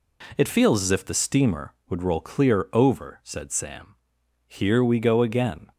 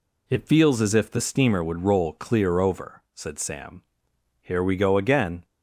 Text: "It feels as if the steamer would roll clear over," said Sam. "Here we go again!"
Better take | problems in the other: neither | none

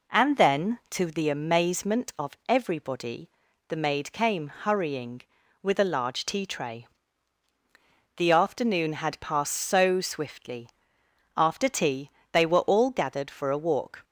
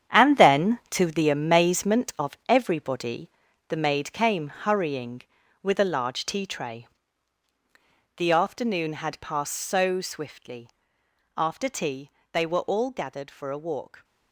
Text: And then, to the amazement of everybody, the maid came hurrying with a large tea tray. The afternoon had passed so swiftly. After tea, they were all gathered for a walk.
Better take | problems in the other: first | gets quieter; strong; throughout; 10.5 dB

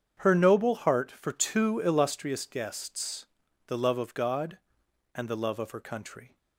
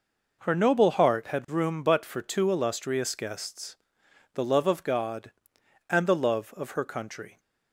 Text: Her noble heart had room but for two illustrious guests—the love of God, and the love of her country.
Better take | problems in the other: second | starts louder than the rest; strong; until 1.2 s; 8 dB // skips "had room but"; at 1.1 s

